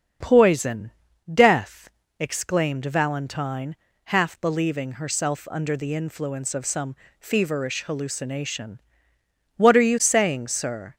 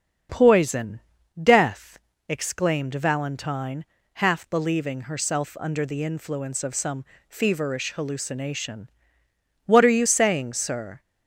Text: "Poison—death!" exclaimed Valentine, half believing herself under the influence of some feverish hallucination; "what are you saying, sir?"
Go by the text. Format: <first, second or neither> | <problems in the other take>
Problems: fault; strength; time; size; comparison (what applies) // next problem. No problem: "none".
neither | starts louder than the rest; the same in both // pauses between "some" and "feverish"; slight; the same in both